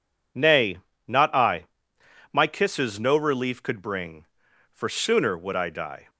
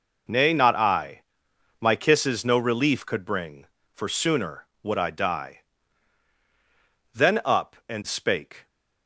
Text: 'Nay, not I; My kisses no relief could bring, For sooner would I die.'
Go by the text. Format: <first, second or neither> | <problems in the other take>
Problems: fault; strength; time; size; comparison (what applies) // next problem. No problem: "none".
first | goes on to say "Then up and spake"; from 7.1 s on; 1.5 s long